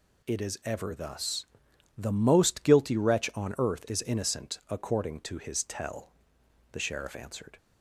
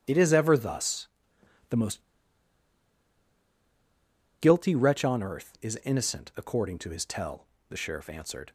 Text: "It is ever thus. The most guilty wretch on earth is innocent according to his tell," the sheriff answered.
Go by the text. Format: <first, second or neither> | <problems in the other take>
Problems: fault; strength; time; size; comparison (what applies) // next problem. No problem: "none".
first | starts louder than the rest; strong; until 1.0 s; 10.5 dB // pauses between "most" and "guilty"; strong; at 2.0 s; 2.3 s long